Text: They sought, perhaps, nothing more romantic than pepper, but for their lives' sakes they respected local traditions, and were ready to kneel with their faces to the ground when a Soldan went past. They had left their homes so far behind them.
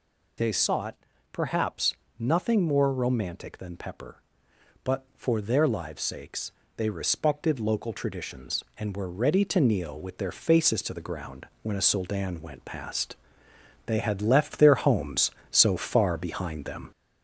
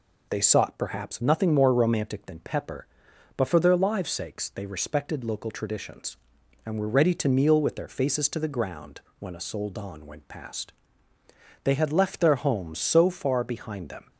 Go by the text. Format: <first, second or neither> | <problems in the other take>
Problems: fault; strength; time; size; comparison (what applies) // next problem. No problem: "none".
second | gets louder; slight; throughout; 2.5 dB // pauses between "sakes" and "they"; slight; at 6.5 s; 0.24 s long // pauses between "ground" and "when"; slight; at 11.4 s; 0.16 s long; slight in the second